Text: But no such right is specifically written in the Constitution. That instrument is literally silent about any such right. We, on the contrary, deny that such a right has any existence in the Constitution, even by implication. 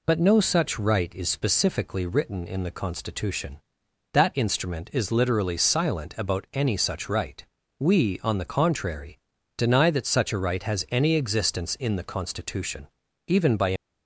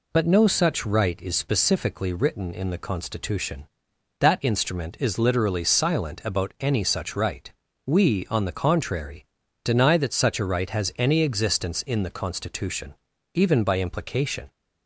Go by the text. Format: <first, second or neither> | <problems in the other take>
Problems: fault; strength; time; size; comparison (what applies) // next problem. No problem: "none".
second | stops before "implication"; at 13.7 s